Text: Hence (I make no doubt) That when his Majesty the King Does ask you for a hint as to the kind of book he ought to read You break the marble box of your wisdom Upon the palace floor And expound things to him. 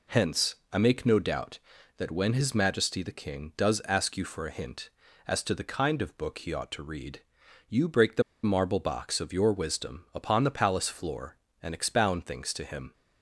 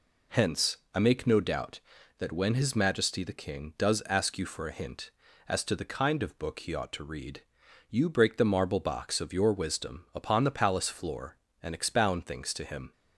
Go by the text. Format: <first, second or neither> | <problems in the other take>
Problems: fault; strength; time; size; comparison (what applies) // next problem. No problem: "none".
second | pauses between "read" and "You"; noticeable; at 7.1 s; 0.48 s long; noticeable in the second // pauses between "the" and "marble"; slight; at 8.2 s; 0.21 s long